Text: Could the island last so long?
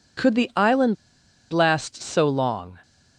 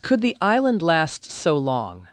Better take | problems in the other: second | pauses between "island" and "last"; noticeable; at 0.9 s; 0.58 s long

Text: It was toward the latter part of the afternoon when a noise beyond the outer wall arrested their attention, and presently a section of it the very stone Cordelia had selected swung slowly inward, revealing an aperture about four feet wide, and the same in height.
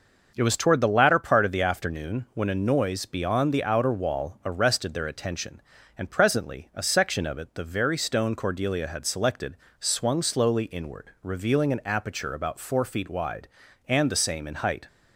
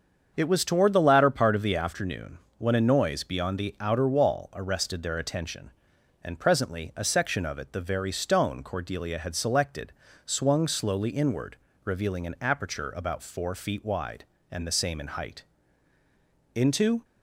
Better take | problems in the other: first | starts louder than the rest; until 1.3 s; 7 dB; noticeable in the first // pauses between "afternoon" and "when"; slight; at 2.3 s; 0.18 s long // pauses between "selected" and "swung"; slight; at 9.9 s; 0.34 s long; slight in the first // goes on to say "Into"; slight; from 16.5 s on; 0.48 s long

